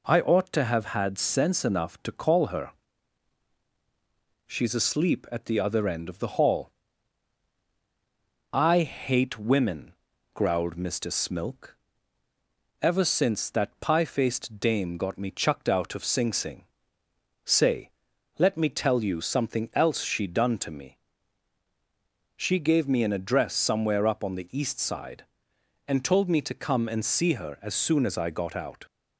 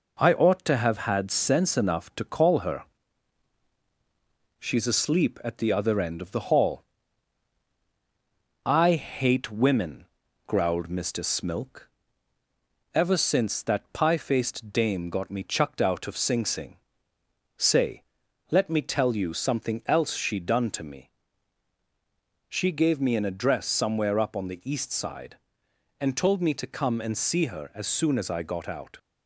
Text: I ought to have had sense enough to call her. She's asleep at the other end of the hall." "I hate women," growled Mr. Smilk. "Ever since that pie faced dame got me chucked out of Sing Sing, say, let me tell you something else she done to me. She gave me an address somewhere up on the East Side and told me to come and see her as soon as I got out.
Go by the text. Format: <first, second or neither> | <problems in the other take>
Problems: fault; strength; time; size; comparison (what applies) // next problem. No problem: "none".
first | gets quieter; slight; throughout; 3 dB